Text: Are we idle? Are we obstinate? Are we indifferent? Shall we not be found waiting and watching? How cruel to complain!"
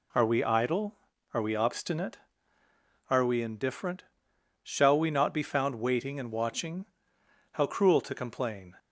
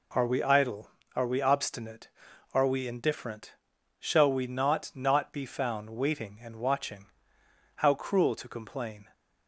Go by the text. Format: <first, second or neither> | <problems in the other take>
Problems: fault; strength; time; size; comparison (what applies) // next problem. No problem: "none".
first | says "not" twice; at 4.9 s